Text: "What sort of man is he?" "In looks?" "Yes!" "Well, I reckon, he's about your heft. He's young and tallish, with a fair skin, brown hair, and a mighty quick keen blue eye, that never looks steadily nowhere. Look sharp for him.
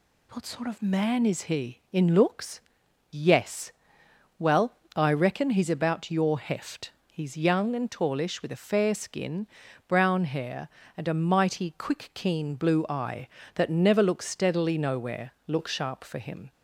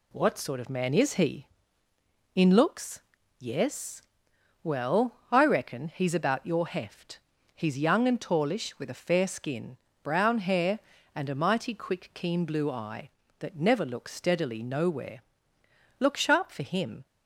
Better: neither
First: none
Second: none

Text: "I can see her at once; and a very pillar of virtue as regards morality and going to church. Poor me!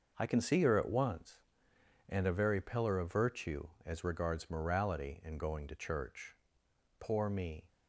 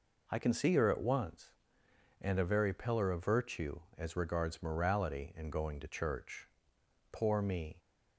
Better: second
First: gets quieter; strong; throughout; 8 dB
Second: none

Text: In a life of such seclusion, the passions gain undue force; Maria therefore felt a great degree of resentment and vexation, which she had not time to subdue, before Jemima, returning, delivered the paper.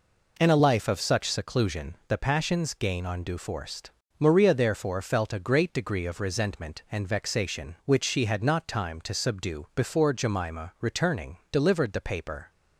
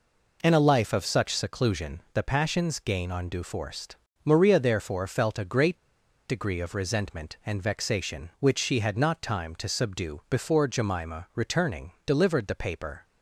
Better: first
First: none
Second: pauses between "great" and "degree"; noticeable; at 5.7 s; 0.49 s long

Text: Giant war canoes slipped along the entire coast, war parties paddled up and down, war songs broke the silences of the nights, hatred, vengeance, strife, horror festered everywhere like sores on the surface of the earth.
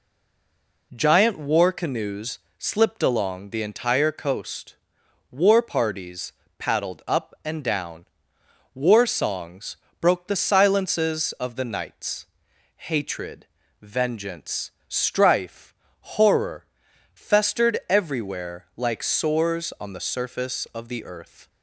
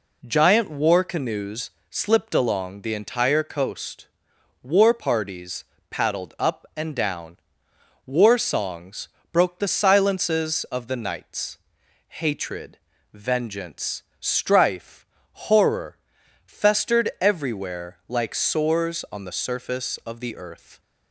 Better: second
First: stays silent before the first word; slight; until 0.9 s; 0.9 s long // pauses between "canoes" and "slipped"; slight; at 2.3 s; 0.18 s long // pauses between "parties" and "paddled"; slight; at 6.3 s; 0.26 s long // pauses between "songs" and "broke"; slight; at 9.7 s; 0.24 s long // pauses between "horror" and "festered"; noticeable; at 16.6 s; 0.48 s long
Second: pauses between "canoes" and "slipped"; slight; at 1.7 s; 0.18 s long // pauses between "parties" and "paddled"; slight; at 5.6 s; 0.26 s long // pauses between "songs" and "broke"; slight; at 9.0 s; 0.24 s long // pauses between "horror" and "festered"; noticeable; at 15.9 s; 0.48 s long

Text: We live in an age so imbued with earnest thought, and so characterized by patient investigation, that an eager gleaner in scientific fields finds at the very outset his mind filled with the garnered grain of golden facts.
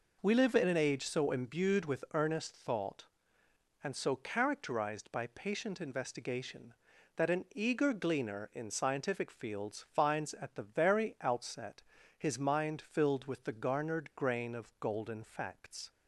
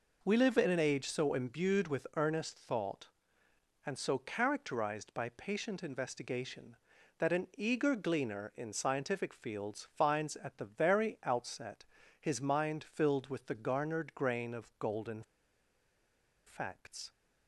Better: first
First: pauses between "outset" and "his"; slight; at 11.8 s; 0.34 s long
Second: pauses between "outset" and "his"; slight; at 11.8 s; 0.34 s long // pauses between "golden" and "facts"; at 15.2 s; 1.2 s long

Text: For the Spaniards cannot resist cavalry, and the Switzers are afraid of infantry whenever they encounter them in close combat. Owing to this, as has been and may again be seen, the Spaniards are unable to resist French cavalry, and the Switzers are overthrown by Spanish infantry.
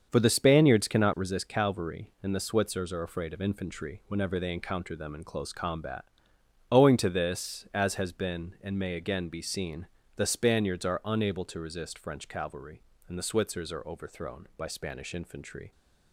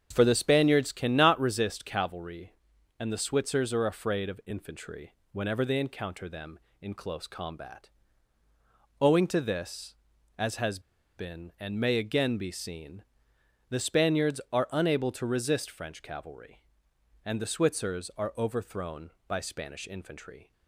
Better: first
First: starts louder than the rest; until 1.1 s; 7 dB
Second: starts louder than the rest; strong; until 1.1 s; 7.5 dB // pauses between "infantry" and "whenever"; slight; at 5.1 s; 0.16 s long // pauses between "has" and "been"; at 10.7 s; 0.37 s long

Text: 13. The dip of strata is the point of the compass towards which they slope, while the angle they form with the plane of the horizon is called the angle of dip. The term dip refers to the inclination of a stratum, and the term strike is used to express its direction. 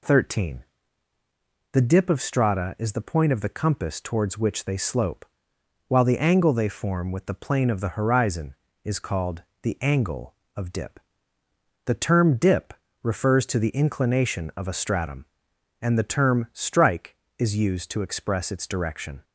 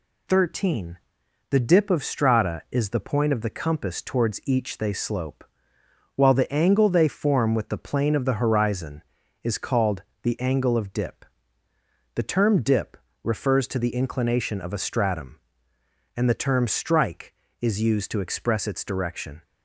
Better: first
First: pauses between "called" and "the"; slight; at 9.4 s; 0.18 s long // pauses between "dip" and "refers"; slight; at 12.7 s; 0.28 s long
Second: says "each" for "which"; at 4.4 s // pauses between "called" and "the"; slight; at 10.0 s; 0.20 s long // pauses between "dip" and "refers"; slight; at 12.9 s; 0.26 s long

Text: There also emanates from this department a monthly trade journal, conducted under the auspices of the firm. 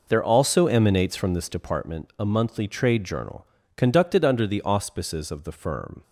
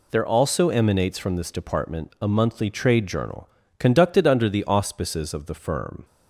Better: second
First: starts louder than the rest; noticeable; until 1.8 s; 5 dB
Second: none

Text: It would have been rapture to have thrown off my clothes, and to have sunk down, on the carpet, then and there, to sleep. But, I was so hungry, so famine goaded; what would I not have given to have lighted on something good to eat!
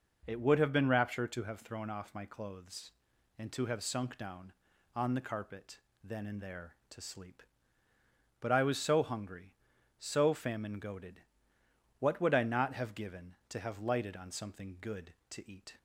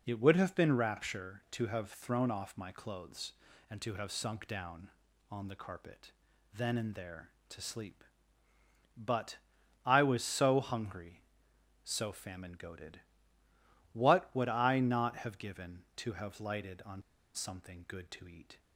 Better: first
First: none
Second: pauses between "on" and "something"; slight; at 17.0 s; 0.32 s long

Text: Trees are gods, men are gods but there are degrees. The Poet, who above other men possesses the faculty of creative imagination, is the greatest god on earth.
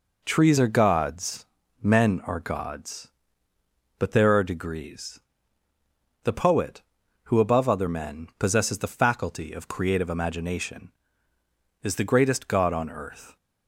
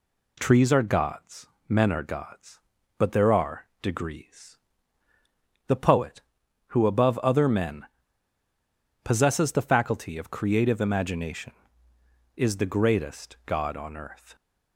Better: first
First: none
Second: pauses between "men" and "possesses"; at 7.8 s; 1.1 s long

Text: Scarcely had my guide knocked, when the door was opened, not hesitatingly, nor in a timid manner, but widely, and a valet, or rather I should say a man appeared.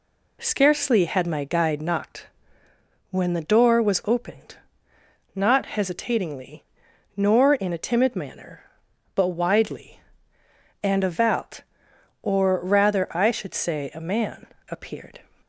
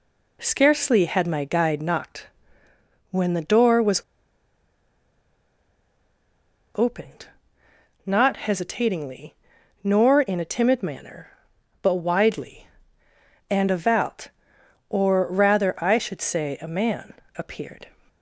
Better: first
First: pauses between "man" and "appeared"; slight; at 14.4 s; 0.22 s long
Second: pauses between "was" and "opened"; strong; at 4.0 s; 2.7 s long // pauses between "man" and "appeared"; slight; at 17.1 s; 0.22 s long

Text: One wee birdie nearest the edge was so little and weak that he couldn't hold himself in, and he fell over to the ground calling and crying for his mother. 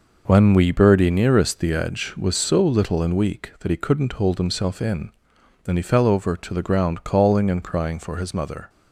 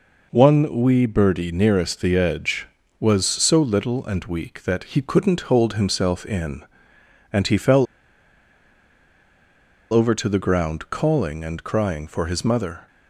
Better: first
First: none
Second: pauses between "fell" and "over"; strong; at 7.8 s; 2.0 s long

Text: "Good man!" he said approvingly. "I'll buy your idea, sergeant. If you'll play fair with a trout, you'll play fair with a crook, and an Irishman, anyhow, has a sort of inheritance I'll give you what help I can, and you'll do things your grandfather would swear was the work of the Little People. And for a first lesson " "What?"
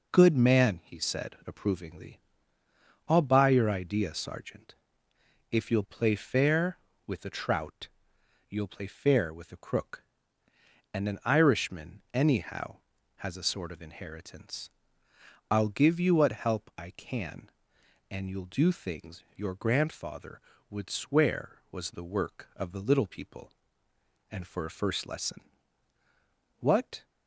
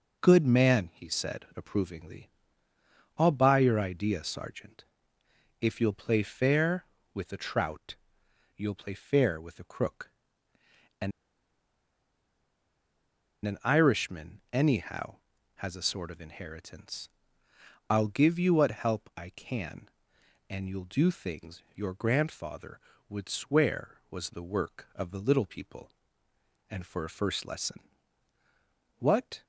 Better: first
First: pauses between "inheritance" and "I'll"; noticeable; at 14.7 s; 0.82 s long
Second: pauses between "and" and "an"; strong; at 11.1 s; 2.3 s long // pauses between "inheritance" and "I'll"; noticeable; at 17.0 s; 0.82 s long

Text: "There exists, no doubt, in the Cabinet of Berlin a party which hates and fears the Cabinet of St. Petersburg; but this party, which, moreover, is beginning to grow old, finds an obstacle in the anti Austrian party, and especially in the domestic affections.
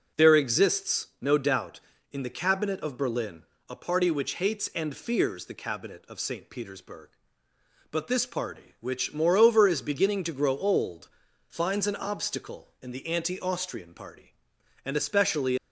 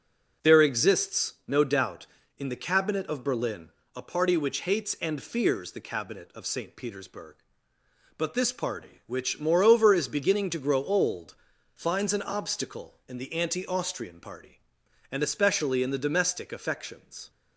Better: second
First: pauses between "Berlin" and "a"; slight; at 3.4 s; 0.24 s long // stops before "in the domestic affections"; at 15.5 s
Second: pauses between "Berlin" and "a"; slight; at 3.6 s; 0.24 s long

